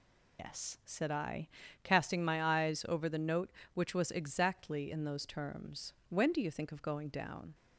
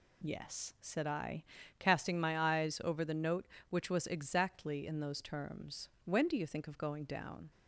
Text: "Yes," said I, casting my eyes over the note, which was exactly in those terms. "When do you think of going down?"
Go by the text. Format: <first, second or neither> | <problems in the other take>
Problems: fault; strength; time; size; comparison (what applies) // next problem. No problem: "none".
second | loses the start of "Yes"; at 0.3 s; 135 ms